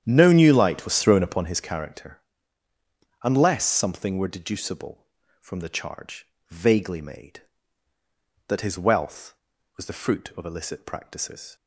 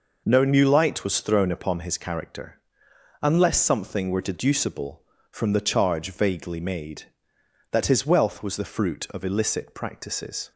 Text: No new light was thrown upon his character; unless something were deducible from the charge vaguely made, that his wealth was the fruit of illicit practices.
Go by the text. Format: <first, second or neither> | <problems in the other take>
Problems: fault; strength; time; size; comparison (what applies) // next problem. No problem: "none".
second | starts louder than the rest; strong; until 1.5 s; 9.5 dB // pauses between "charge" and "vaguely"; slight; at 6.2 s; 0.22 s long